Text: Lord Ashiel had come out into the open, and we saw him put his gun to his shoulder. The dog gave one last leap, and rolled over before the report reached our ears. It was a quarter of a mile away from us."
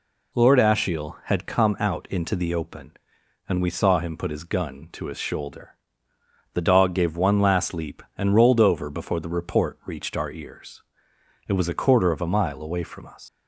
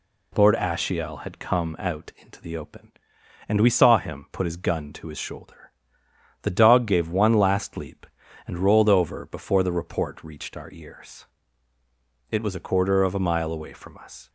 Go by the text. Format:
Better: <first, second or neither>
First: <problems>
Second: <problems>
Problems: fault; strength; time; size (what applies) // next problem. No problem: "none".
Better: second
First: leaves "us" unfinished; at 13.2 s; 140 ms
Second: none